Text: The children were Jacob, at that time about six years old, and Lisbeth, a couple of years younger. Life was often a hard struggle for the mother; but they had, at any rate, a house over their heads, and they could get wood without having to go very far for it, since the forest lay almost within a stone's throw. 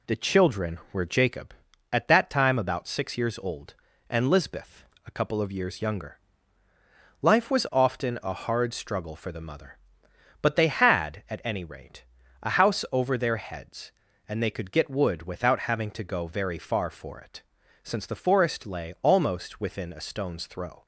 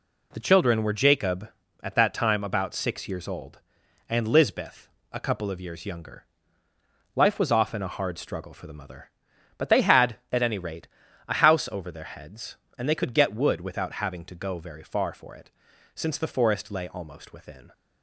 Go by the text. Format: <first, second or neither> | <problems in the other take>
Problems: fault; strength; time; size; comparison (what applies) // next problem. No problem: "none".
first | stops before "a stone's throw"; at 17.7 s